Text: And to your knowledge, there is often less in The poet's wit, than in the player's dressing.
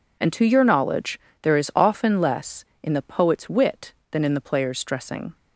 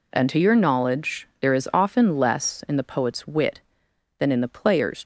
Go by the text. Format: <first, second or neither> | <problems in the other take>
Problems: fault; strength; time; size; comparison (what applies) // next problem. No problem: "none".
first | stops before "dressing"; at 5.0 s